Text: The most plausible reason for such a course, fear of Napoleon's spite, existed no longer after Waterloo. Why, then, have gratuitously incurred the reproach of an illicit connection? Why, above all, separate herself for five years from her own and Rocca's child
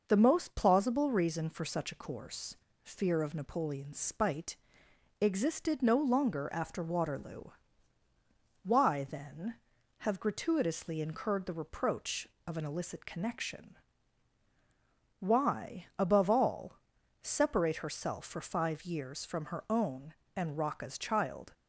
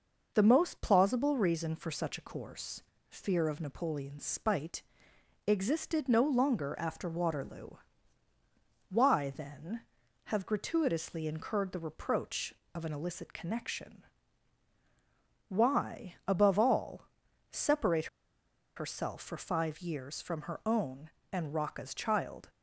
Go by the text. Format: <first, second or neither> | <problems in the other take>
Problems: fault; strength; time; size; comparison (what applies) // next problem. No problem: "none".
first | pauses between "separate" and "herself"; noticeable; at 18.0 s; 0.70 s long